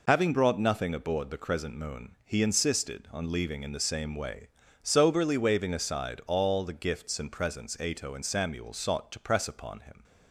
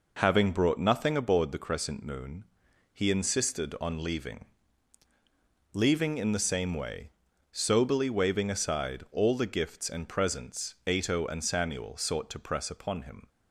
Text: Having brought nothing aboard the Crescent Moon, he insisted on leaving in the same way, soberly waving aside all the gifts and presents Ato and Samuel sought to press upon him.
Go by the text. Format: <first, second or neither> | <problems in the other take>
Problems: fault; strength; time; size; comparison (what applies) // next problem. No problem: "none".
first | says "leaving" twice; at 5.7 s